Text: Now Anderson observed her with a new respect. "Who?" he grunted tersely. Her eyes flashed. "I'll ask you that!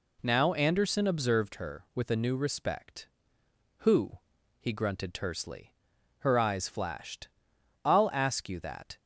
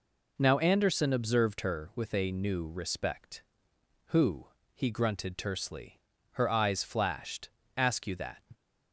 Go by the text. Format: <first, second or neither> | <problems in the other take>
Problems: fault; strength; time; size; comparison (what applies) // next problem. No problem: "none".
first | skips "I'll"; at 7.6 s